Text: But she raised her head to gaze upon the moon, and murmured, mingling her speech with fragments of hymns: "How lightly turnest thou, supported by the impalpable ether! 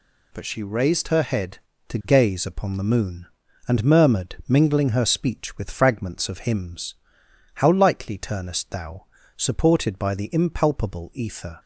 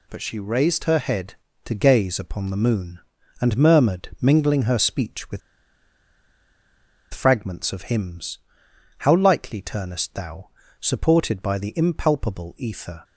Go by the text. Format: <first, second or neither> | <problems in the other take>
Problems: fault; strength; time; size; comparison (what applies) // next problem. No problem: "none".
first | pauses between "with" and "fragments"; strong; at 5.4 s; 1.7 s long